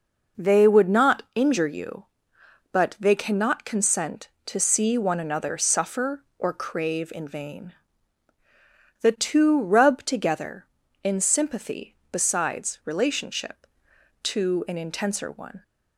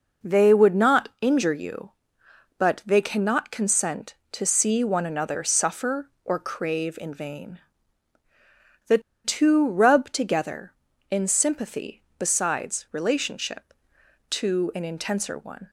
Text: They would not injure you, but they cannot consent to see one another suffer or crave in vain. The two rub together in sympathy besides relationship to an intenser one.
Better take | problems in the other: first | pauses between "The" and "two"; slight; at 8.9 s; 0.25 s long

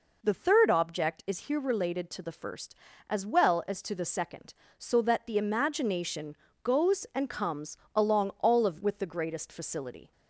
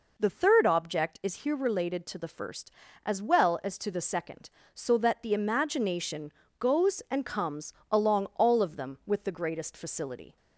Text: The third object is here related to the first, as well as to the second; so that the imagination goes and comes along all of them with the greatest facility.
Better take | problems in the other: second | pauses between "imagination" and "goes"; slight; at 6.3 s; 0.30 s long; slight in the second // pauses between "comes" and "along"; slight; at 7.7 s; 0.18 s long; slight in the second // skips "them"; at 8.8 s

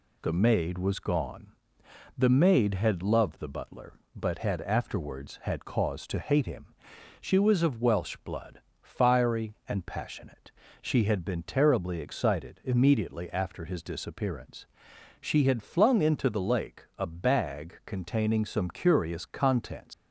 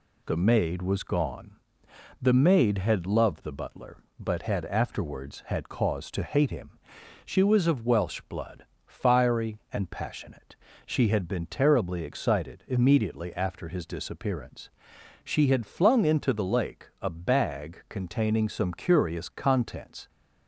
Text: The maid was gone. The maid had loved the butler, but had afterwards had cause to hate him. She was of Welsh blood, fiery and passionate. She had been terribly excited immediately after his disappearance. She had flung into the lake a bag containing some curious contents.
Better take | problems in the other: second | leaves "contents" unfinished; at 19.9 s; 110 ms

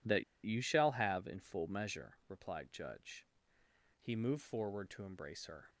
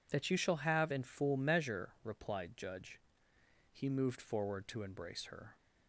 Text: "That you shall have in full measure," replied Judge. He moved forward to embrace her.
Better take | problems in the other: second | pauses between "That" and "you"; slight; at 0.2 s; 0.21 s long

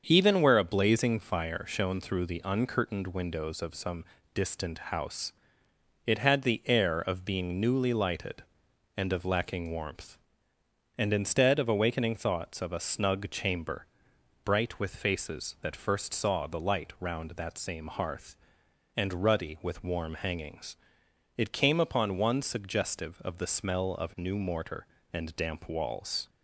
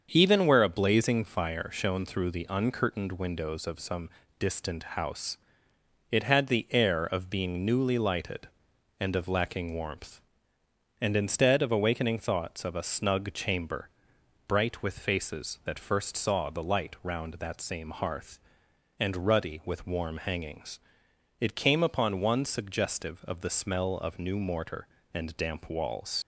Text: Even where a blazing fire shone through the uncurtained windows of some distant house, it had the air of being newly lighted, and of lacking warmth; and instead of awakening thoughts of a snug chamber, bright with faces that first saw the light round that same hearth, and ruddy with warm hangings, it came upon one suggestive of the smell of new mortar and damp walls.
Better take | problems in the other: first | starts louder than the rest; until 1.1 s; 7 dB; also in the first // pauses between "some" and "distant"; slight; at 4.0 s; 0.30 s long; slight in the first // pauses between "distant" and "house"; slight; at 4.8 s; 0.16 s long; slight in the first // leaves "walls" unfinished; at 26.2 s; 75 ms

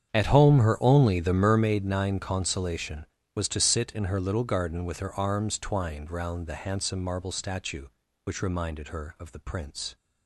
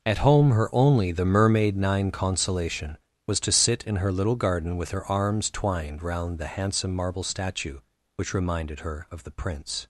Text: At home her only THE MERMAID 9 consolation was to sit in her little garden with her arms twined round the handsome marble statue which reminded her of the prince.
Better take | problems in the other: second | starts louder than the rest; strong; until 1.5 s; 8 dB

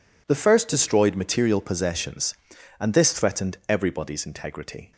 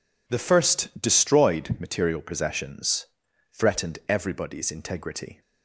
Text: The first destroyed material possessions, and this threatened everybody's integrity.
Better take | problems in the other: first | skips "and this"; at 3.2 s

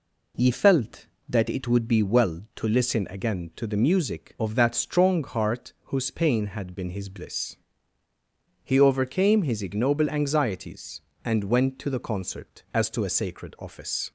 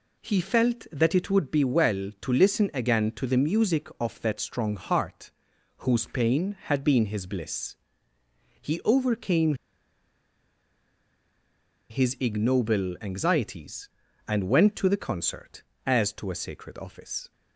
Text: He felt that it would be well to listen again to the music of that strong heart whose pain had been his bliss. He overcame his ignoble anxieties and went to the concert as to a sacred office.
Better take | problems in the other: first | pauses between "heart" and "whose"; noticeable; at 5.2 s; 0.48 s long // pauses between "overcame" and "his"; strong; at 9.5 s; 2.3 s long

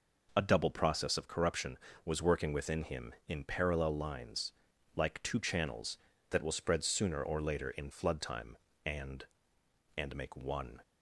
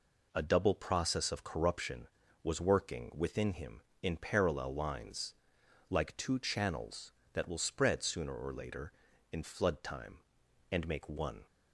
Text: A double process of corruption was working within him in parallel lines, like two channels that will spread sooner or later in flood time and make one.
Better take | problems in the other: second | says "and" twice; at 9.9 s

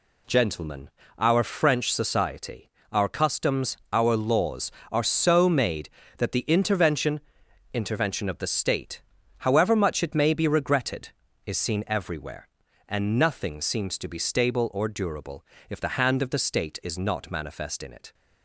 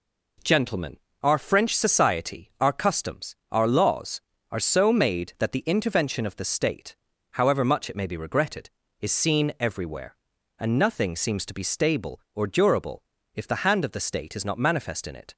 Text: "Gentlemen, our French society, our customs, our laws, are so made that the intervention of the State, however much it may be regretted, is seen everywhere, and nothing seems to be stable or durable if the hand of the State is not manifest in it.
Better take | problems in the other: second | says "intervention" twice; at 7.7 s // pauses between "durable" and "if"; slight; at 15.4 s; 0.26 s long; slight in the second

